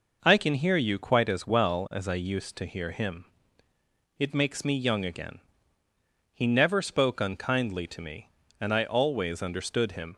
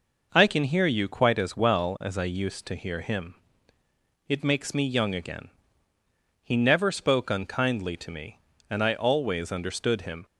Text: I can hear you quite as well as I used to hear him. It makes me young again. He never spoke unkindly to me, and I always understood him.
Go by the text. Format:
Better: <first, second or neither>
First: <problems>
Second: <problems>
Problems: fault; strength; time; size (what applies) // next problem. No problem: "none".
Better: neither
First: none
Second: none